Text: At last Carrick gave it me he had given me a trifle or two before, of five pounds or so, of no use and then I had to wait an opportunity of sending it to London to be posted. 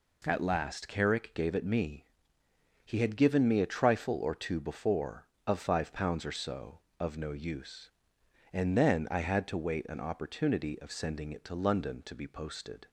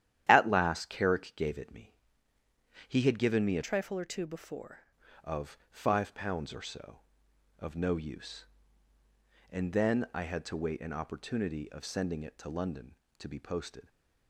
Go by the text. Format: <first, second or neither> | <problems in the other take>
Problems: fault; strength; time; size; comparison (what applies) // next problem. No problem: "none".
first | starts louder than the rest; strong; until 1.3 s; 11 dB // pauses between "me" and "he"; noticeable; at 1.9 s; 0.94 s long; noticeable in the first // changes voice from "trifle" to "before"; from 3.6 to 4.8 s; 1.2 s long